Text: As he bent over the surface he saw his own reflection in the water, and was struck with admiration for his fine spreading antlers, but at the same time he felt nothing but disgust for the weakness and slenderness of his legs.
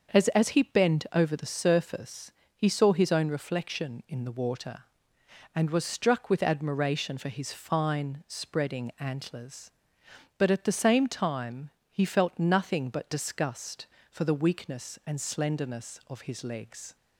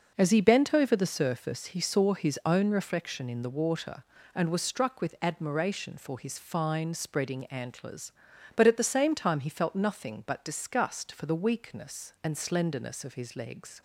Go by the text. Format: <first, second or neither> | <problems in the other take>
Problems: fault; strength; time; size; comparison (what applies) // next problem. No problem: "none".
second | starts louder than the rest; until 1.2 s; 6 dB // says "As" twice; at 0.2 s // pauses between "surface" and "he"; slight; at 2.3 s; 0.24 s long // pauses between "time" and "he"; slight; at 11.6 s; 0.22 s long